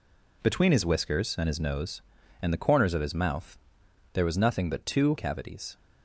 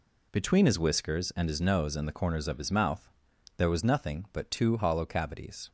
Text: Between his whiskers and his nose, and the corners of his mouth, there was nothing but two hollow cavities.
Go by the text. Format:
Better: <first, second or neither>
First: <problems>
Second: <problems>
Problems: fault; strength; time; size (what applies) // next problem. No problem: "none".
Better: second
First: skips "hollow"; at 5.1 s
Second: none